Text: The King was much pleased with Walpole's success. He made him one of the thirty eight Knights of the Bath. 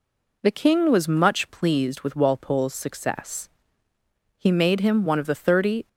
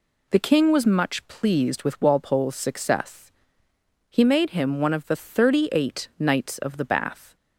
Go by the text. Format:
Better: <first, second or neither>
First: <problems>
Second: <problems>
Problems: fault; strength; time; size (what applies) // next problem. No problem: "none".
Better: second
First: stops before "eight Knights of the Bath"; at 5.8 s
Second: none